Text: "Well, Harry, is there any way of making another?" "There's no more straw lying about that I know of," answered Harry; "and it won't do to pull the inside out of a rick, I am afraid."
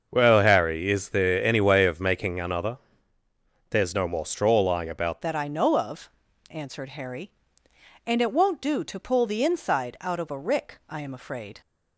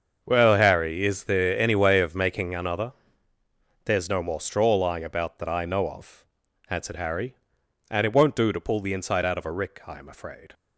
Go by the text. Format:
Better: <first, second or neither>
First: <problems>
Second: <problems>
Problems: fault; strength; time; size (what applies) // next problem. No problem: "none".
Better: second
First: starts louder than the rest; until 1.1 s; 6.5 dB // changes voice at "that"; from 5.2 s on; 6.4 s long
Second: starts louder than the rest; until 1.2 s; 6.5 dB